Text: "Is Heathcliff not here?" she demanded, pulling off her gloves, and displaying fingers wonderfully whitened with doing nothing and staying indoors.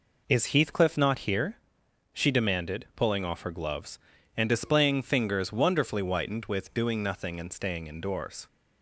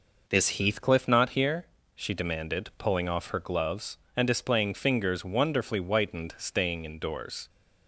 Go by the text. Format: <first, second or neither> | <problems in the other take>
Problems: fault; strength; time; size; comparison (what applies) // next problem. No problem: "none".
first | skips "with doing nothing and"; at 6.3 s